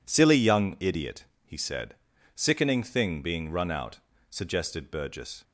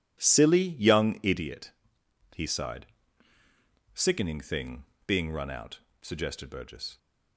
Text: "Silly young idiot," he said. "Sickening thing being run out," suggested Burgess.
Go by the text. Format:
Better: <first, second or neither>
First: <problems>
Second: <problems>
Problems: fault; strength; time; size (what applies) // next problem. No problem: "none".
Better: first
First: none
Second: says "sighed" for "said"; at 2.4 s // pauses between "thing" and "being"; slight; at 4.8 s; 0.22 s long